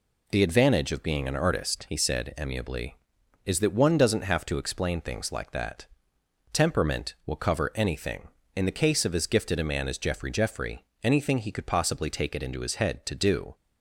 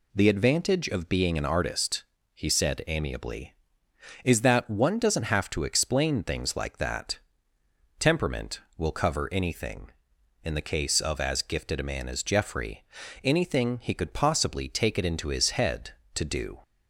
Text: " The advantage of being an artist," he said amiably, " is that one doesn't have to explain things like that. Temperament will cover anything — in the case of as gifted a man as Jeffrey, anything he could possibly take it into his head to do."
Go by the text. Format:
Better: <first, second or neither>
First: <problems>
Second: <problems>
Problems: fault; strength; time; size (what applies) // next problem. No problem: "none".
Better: second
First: says "Jeffrey" twice; at 10.3 s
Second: none